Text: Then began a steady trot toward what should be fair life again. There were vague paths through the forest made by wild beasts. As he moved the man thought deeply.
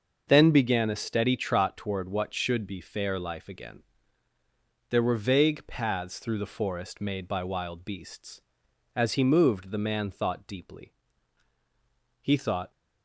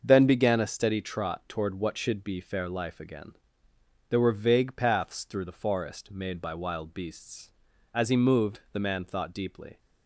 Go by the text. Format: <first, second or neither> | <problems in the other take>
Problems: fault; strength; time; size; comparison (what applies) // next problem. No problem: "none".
second | starts louder than the rest; until 1.2 s; 6 dB; also in the second // goes on to say "He thought"; from 12.2 s on; 0.50 s long